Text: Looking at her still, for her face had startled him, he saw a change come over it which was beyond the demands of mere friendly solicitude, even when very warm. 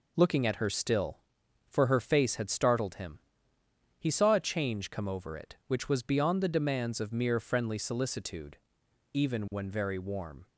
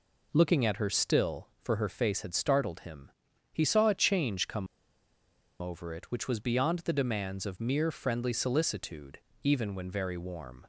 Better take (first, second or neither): first